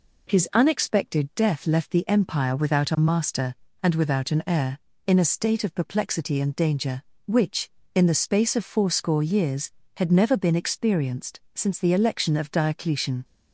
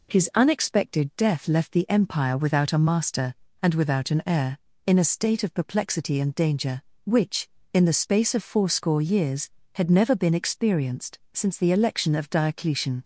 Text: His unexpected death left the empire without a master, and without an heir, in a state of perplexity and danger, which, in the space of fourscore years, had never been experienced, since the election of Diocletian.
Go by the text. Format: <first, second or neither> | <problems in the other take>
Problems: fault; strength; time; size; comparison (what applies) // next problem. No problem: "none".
neither | none